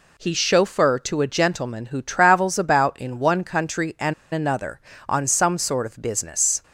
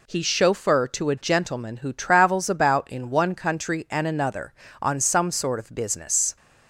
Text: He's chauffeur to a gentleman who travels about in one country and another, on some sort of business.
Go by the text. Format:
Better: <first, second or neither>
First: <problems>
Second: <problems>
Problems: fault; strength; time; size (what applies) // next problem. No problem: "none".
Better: second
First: pauses between "and" and "another"; slight; at 4.1 s; 0.20 s long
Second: none